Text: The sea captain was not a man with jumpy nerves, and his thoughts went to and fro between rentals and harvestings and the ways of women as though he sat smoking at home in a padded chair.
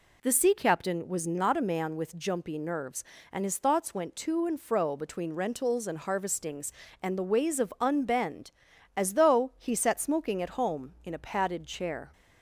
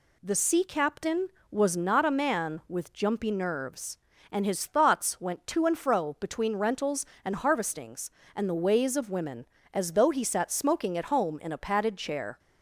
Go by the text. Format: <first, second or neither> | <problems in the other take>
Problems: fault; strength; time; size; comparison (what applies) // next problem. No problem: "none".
second | says "unbend" for "women"; at 7.7 s